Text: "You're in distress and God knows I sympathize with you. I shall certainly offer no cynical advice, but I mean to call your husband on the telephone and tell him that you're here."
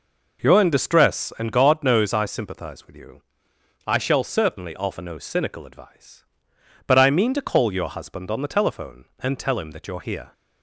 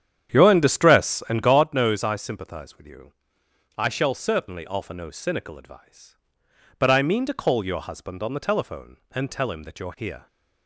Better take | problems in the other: first | starts louder than the rest; strong; until 1.7 s; 9 dB

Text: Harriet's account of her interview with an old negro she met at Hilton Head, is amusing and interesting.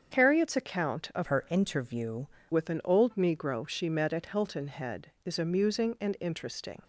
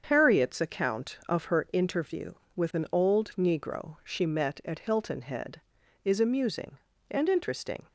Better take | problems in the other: second | starts louder than the rest; strong; until 1.1 s; 7.5 dB; strong in the second // changes voice from "her" to "interview"; from 1.2 to 2.2 s; 1.0 s long

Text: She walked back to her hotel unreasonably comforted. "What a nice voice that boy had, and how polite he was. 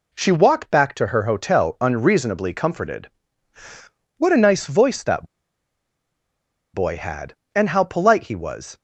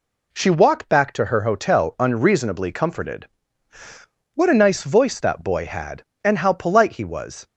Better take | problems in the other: second | pauses between "that" and "boy"; strong; at 5.2 s; 1.4 s long

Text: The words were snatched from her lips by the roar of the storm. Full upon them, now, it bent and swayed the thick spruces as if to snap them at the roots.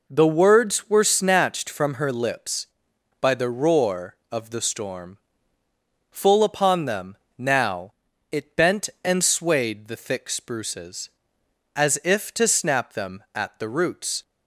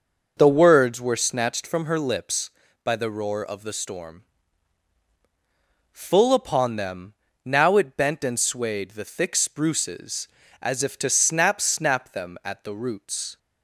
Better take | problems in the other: first | says "snap" twice; at 11.6 s

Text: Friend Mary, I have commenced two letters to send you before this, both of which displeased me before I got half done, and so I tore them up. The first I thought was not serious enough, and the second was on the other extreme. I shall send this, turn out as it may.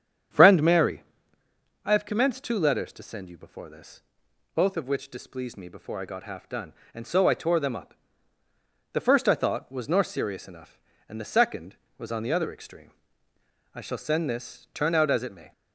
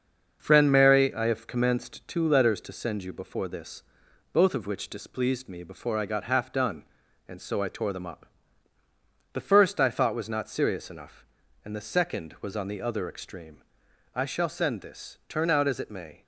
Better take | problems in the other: second | starts louder than the rest; strong; until 2.1 s; 8.5 dB; also in the second // says "nor" for "not"; at 9.8 s

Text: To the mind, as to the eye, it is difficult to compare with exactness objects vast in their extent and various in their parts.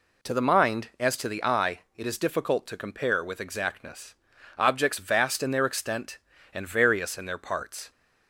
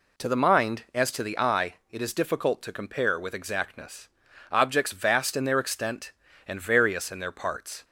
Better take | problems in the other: neither | pauses between "exactness" and "objects"; the same in both

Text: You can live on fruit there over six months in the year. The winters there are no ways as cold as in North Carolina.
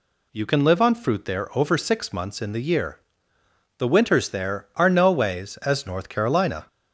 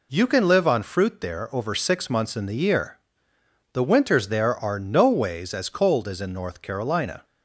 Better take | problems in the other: second | skips "cold as in"; at 5.8 s

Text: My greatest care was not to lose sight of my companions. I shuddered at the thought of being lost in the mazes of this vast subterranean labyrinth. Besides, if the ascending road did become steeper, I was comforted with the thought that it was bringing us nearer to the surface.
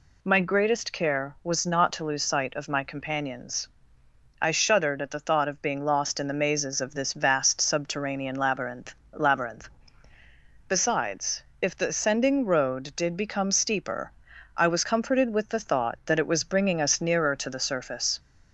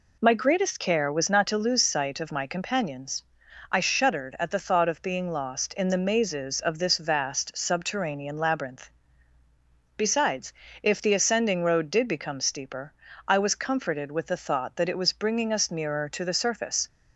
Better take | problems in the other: second | says "labyrinth" twice; at 9.1 s

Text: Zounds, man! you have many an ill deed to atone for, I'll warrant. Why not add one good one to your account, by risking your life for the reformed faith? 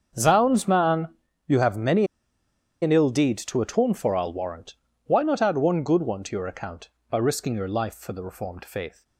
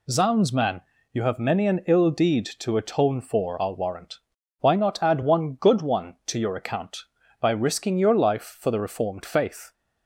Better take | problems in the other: second | starts louder than the rest; until 1.5 s; 7 dB // pauses between "many" and "an"; noticeable; at 2.0 s; 0.76 s long

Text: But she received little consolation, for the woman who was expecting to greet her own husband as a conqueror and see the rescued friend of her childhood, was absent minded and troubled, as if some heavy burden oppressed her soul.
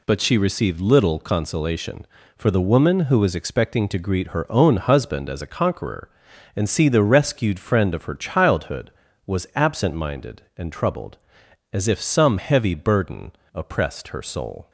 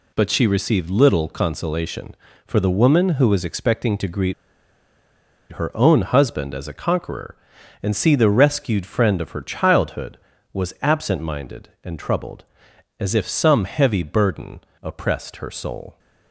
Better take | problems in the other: first | pauses between "greet" and "her"; at 4.3 s; 1.1 s long // pauses between "burden" and "oppressed"; slight; at 14.6 s; 0.22 s long; slight in the first

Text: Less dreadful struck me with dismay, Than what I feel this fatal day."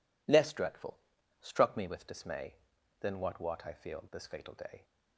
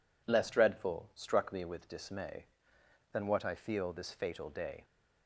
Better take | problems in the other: second | pauses between "dreadful" and "struck"; at 0.9 s; 0.42 s long // says "what" twice; at 3.4 s

